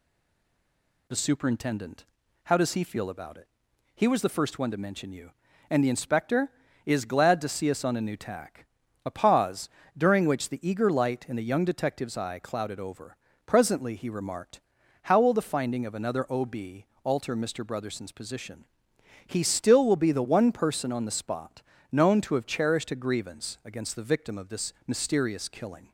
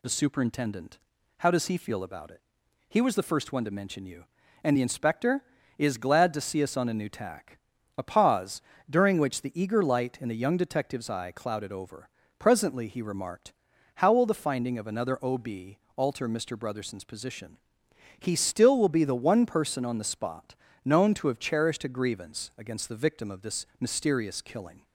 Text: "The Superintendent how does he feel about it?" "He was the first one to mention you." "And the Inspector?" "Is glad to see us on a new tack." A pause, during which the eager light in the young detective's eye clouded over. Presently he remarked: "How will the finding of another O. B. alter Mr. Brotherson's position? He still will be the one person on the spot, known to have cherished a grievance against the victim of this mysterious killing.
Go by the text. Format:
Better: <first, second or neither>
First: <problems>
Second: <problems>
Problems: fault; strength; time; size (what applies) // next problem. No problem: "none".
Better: second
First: stays silent before the first word; until 1.0 s; 1.0 s long // pauses between "Superintendent" and "how"; at 2.0 s; 0.40 s long // pauses between "B" and "alter"; slight; at 16.8 s; 0.18 s long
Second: pauses between "Superintendent" and "how"; at 0.9 s; 0.40 s long // pauses between "B" and "alter"; slight; at 15.7 s; 0.18 s long